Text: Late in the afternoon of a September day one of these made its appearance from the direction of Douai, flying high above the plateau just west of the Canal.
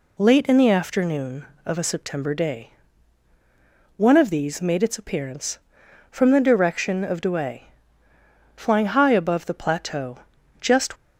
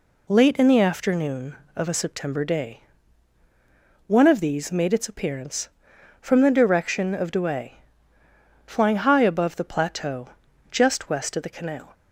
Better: second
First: pauses between "day" and "one"; strong; at 2.6 s; 1.2 s long // pauses between "plateau" and "just"; at 10.1 s; 0.42 s long // stops before "west of the Canal"; at 10.9 s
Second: pauses between "day" and "one"; strong; at 2.7 s; 1.2 s long // pauses between "plateau" and "just"; at 10.2 s; 0.42 s long

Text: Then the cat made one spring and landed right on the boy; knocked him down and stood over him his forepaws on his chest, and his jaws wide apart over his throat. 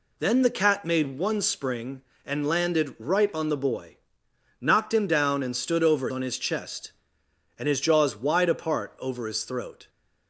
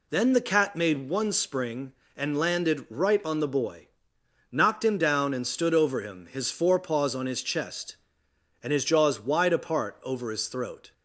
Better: second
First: skips "him his forepaws"; at 6.0 s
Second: none

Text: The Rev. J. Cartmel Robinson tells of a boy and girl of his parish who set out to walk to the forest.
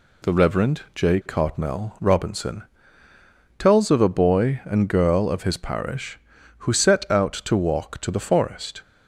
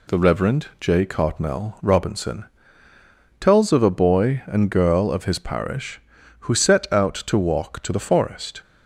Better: neither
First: pauses between "Robinson" and "tells"; noticeable; at 2.6 s; 0.96 s long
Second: pauses between "Robinson" and "tells"; noticeable; at 2.4 s; 0.96 s long

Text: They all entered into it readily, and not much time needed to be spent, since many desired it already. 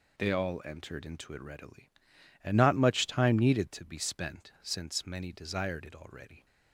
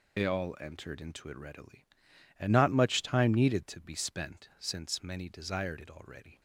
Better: first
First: none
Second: loses the start of "They"; at 0.1 s; 45 ms

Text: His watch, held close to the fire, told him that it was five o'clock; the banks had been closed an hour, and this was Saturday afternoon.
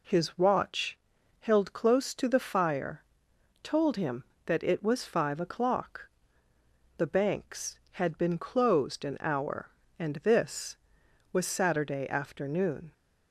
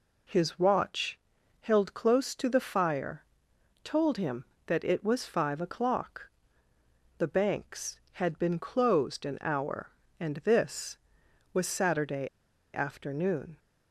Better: first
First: none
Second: pauses between "Saturday" and "afternoon"; at 12.2 s; 0.45 s long

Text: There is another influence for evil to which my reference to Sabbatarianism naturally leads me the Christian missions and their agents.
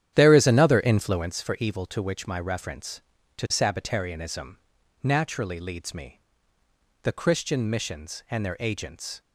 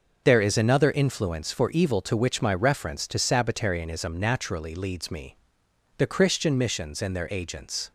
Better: second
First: starts louder than the rest; strong; until 1.4 s; 10.5 dB // pauses between "Sabbatarianism" and "naturally"; noticeable; at 4.5 s; 0.46 s long // pauses between "me" and "the"; noticeable; at 6.2 s; 0.80 s long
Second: pauses between "me" and "the"; noticeable; at 5.3 s; 0.60 s long

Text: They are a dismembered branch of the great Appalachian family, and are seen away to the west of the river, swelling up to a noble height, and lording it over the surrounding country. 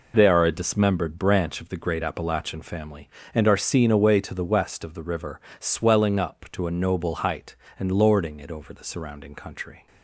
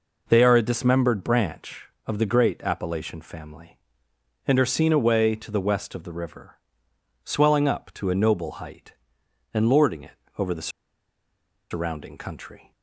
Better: first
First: none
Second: pauses between "it" and "over"; slight; at 10.1 s; 0.20 s long // pauses between "the" and "surrounding"; at 10.6 s; 1.0 s long

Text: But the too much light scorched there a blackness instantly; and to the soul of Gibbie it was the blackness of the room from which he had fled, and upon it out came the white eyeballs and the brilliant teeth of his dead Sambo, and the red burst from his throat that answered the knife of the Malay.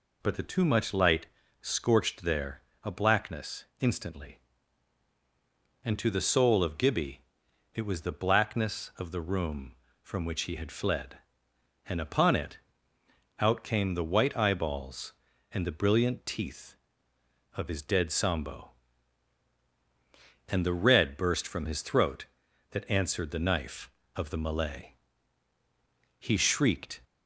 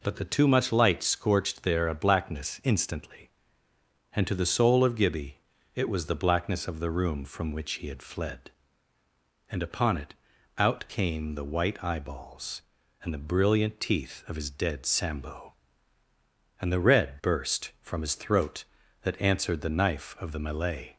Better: second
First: pauses between "light" and "scorched"; slight; at 1.2 s; 0.36 s long // pauses between "there" and "a"; slight; at 2.6 s; 0.20 s long // pauses between "blackness" and "instantly"; slight; at 3.6 s; 0.16 s long // pauses between "Gibbie" and "it"; noticeable; at 7.2 s; 0.52 s long // pauses between "it" and "out"; noticeable; at 12.5 s; 0.80 s long // goes on to say "He shrieked"; noticeable; from 26.1 s on; 0.82 s long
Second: pauses between "Gibbie" and "it"; at 5.3 s; 0.38 s long // pauses between "it" and "out"; at 10.1 s; 0.42 s long

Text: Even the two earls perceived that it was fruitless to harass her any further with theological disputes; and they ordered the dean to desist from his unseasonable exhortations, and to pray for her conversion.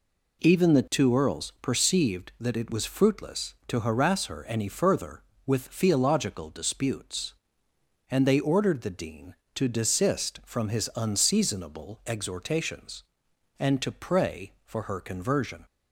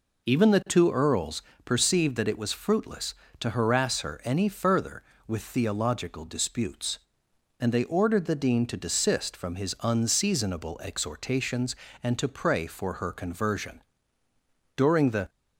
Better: first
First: none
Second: pauses between "earls" and "perceived"; slight; at 1.4 s; 0.24 s long // goes on to say "During the"; from 14.7 s on; 0.52 s long

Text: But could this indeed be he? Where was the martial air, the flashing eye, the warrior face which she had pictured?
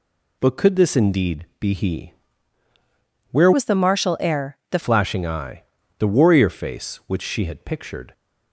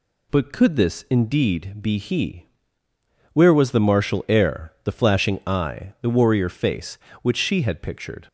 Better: second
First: changes voice from "was" to "the"; from 3.5 to 4.7 s; 1.2 s long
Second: none

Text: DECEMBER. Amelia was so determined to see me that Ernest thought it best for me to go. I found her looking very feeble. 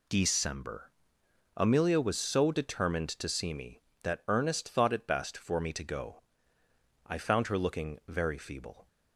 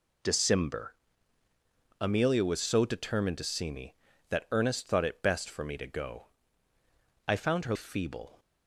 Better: first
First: none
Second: skips "looking very"; at 7.7 s

